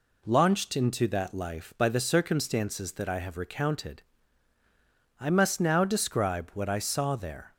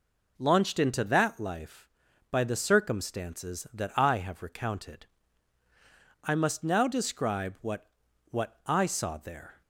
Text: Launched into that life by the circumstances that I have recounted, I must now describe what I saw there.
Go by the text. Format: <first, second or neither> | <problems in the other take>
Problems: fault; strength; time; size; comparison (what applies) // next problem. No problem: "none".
first | says "what" twice; at 8.3 s